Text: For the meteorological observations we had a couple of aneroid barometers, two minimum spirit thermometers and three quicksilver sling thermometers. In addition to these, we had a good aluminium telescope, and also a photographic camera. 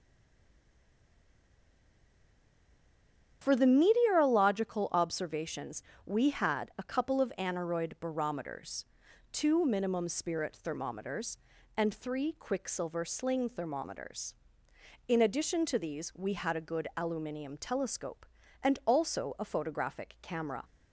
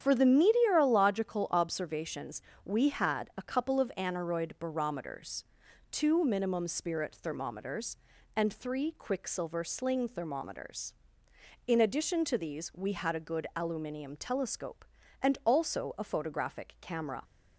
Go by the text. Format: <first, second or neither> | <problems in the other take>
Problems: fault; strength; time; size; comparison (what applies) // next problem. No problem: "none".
second | stays silent before the first word; strong; until 3.4 s; 3.4 s long // starts louder than the rest; strong; until 4.4 s; 8.5 dB; strong in the second // pauses between "observations" and "we"; slight; at 5.8 s; 0.24 s long; slight in the second